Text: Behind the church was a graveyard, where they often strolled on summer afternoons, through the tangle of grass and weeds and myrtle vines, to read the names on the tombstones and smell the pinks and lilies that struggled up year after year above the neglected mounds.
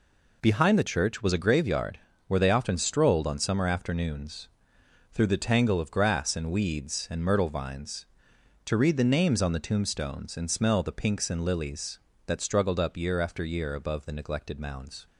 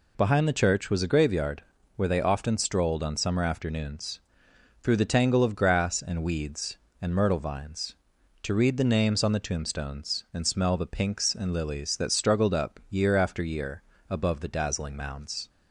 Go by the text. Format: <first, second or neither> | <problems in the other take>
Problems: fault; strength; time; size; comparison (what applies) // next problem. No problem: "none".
first | pauses between "year" and "above"; slight; at 13.8 s; 0.28 s long // says "dazzling" for "neglected"; at 14.4 s